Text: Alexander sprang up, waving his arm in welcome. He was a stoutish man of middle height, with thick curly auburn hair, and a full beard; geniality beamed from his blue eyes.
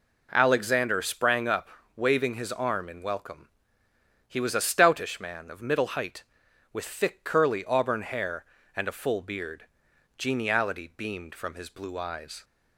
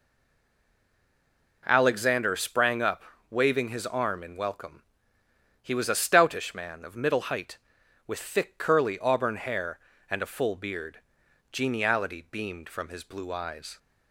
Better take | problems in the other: first | stays silent before the first word; noticeable; until 1.6 s; 1.6 s long

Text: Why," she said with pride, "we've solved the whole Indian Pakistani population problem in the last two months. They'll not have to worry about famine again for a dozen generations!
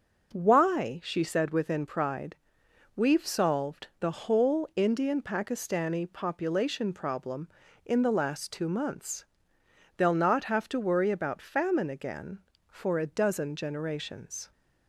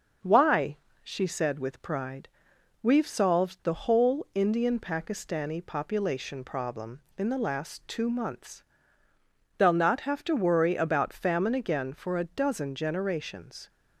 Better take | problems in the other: second | starts louder than the rest; until 1.3 s; 6 dB; also in the second // says "within" for "with"; at 1.4 s

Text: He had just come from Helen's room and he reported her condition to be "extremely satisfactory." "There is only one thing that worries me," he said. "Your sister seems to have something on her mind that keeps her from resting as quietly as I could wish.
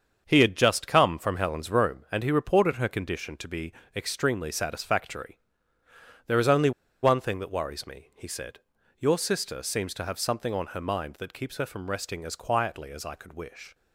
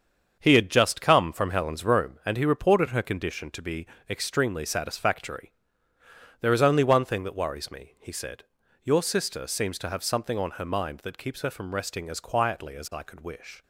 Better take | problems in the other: second | starts louder than the rest; until 1.2 s; 7 dB; also in the second // pauses between "be" and "extremely"; slight; at 3.7 s; 0.22 s long; slight in the second // pauses between "only" and "one"; slight; at 6.7 s; 0.31 s long

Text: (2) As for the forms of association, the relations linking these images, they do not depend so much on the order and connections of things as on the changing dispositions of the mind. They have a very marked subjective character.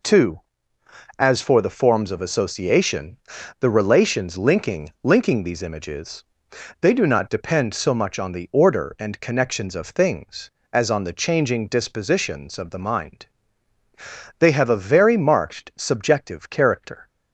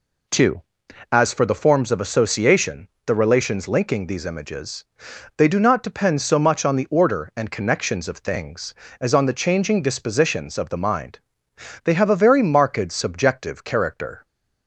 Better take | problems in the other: second | says "linking" twice; at 5.0 s

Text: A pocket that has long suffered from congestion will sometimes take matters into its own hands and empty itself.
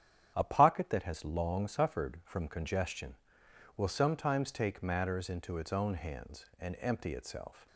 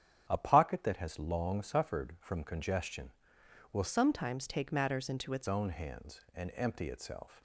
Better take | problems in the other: first | starts louder than the rest; strong; until 1.3 s; 9 dB; strong in the first // changes voice from "sometimes" to "its"; from 3.8 to 5.4 s; 1.6 s long

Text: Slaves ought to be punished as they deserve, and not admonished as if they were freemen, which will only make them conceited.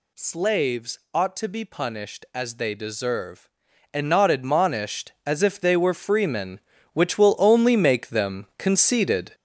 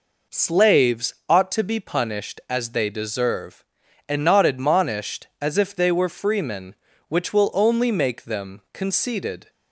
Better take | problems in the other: second | gets louder; strong; throughout; 7.5 dB

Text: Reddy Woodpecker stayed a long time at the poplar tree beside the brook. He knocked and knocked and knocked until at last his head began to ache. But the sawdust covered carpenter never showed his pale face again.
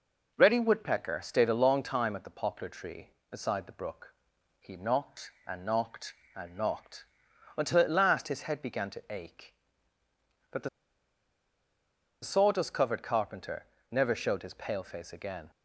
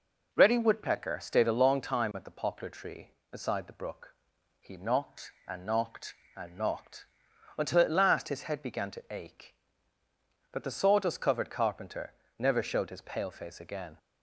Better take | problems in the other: second | pauses between "knocked" and "until"; noticeable; at 7.0 s; 0.50 s long; noticeable in the second // pauses between "the" and "sawdust"; strong; at 10.6 s; 1.5 s long // pauses between "carpenter" and "never"; slight; at 13.6 s; 0.26 s long; slight in the second

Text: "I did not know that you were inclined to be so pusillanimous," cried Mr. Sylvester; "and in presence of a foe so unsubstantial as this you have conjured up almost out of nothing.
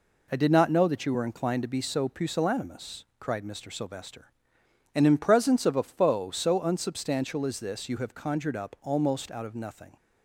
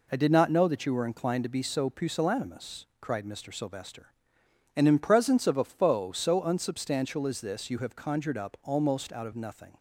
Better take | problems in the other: neither | none

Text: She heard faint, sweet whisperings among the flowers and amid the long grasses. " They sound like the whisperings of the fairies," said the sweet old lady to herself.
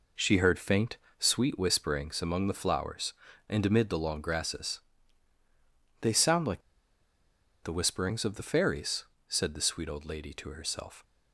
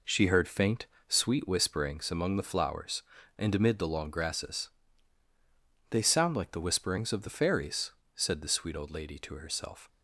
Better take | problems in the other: second | pauses between "like" and "the"; at 6.6 s; 1.0 s long

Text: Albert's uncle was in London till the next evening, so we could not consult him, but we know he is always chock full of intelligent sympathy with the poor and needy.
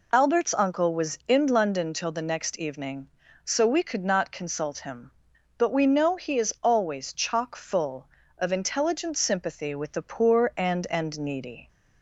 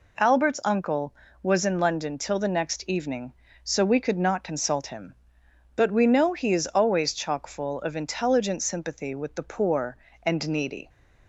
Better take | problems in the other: second | says "and" twice; at 10.9 s

